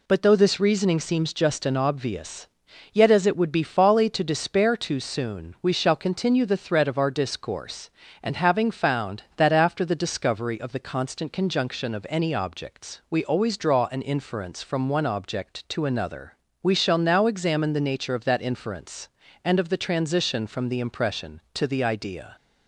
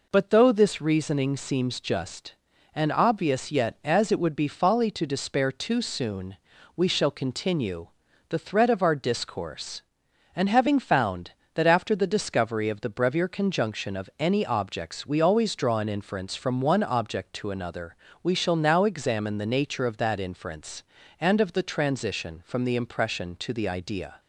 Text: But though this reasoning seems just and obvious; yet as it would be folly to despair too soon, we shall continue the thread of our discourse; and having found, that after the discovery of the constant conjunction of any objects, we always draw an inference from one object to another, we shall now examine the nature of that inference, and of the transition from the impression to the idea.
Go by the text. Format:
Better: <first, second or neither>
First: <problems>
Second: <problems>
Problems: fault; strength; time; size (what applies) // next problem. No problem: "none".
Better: first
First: none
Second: pauses between "continue" and "the"; at 7.8 s; 0.42 s long // says "brevier" for "constant"; at 12.8 s